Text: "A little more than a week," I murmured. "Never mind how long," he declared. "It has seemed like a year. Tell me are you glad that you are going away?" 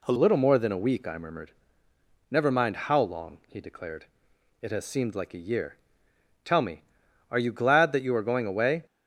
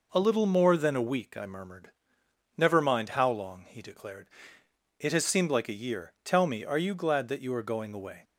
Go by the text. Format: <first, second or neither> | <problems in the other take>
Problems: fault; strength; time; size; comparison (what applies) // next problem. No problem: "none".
second | changes voice at "little"; from 0.1 s on; 8.7 s long